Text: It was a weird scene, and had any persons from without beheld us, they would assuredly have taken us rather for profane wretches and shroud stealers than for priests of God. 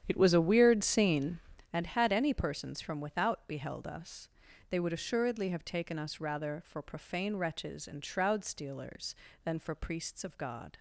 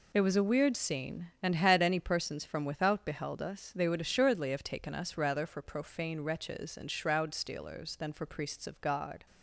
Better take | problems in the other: second | starts louder than the rest; strong; until 1.7 s; 9.5 dB

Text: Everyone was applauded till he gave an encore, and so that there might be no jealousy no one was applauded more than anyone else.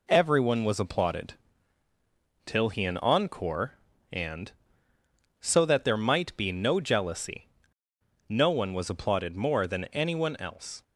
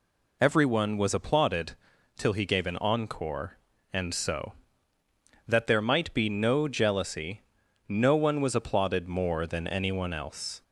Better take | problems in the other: second | pauses between "applauded" and "till"; at 1.3 s; 1.1 s long; also in the second // skips "gave"; at 2.8 s // pauses between "jealousy" and "no"; noticeable; at 7.4 s; 0.80 s long; noticeable in the second

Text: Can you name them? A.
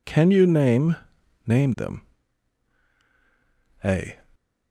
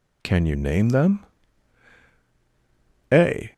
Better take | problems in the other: second | says "name" twice; at 1.4 s

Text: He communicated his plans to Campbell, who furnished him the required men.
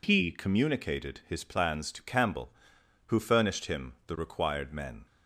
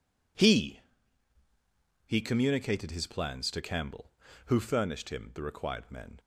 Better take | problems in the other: first | says "He" twice; at 2.0 s

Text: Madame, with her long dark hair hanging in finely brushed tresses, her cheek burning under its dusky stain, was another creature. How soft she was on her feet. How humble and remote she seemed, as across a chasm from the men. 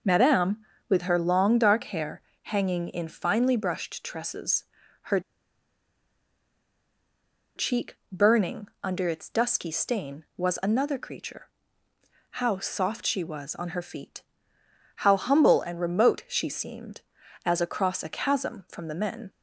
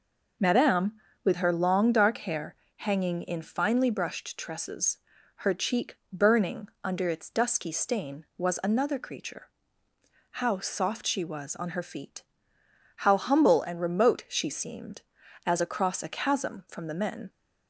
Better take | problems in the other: second | pauses between "hair" and "hanging"; slight; at 2.2 s; 0.24 s long; slight in the second // pauses between "her" and "cheek"; strong; at 5.2 s; 2.3 s long // pauses between "cheek" and "burning"; slight; at 7.9 s; 0.16 s long; slight in the second

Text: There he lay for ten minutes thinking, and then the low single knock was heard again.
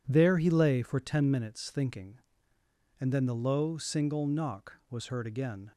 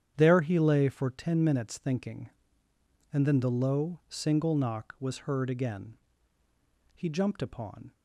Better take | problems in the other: first | starts louder than the rest; strong; until 1.1 s; 9 dB // goes on to say "He jumped upon"; noticeable; from 6.9 s on; 0.98 s long

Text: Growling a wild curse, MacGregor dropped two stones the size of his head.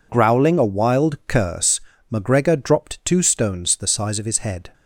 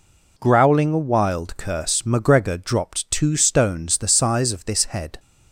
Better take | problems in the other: first | says "this" for "his"; at 4.6 s

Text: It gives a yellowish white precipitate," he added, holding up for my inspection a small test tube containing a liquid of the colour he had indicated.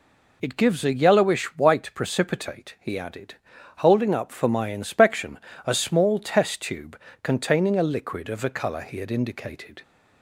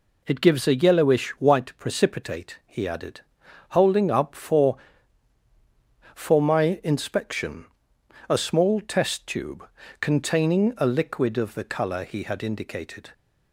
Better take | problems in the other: first | says "for" twice; at 6.1 s // pauses between "inspection" and "a"; noticeable; at 7.6 s; 0.64 s long; slight in the first // pauses between "tube" and "containing"; slight; at 9.6 s; 0.32 s long; slight in the first

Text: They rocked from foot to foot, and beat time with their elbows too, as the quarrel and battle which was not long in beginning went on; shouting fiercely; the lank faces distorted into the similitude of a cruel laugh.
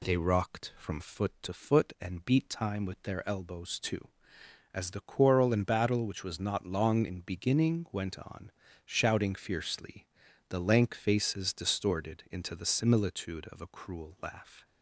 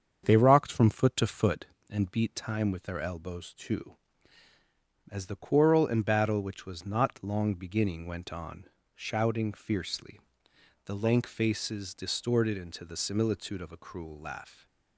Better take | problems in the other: first | starts louder than the rest; strong; until 1.2 s; 7.5 dB // skips "in"; at 7.5 s

